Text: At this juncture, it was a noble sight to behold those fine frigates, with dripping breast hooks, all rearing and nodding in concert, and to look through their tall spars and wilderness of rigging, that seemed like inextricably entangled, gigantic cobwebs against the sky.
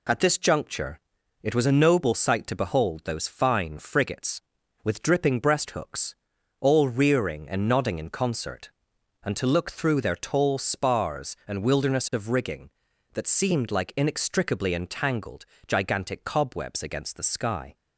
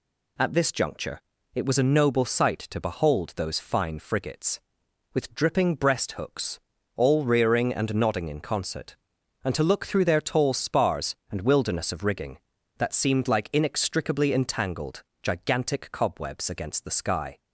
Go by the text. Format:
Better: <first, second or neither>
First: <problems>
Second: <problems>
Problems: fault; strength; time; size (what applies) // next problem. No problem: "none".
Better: neither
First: none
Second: none